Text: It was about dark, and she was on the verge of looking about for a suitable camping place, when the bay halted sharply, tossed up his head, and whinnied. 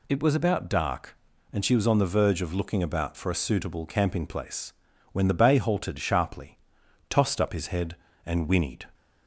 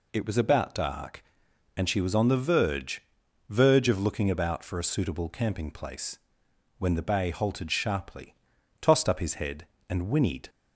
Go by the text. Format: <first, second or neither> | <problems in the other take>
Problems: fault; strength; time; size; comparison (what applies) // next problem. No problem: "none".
first | says "verge" twice; at 3.4 s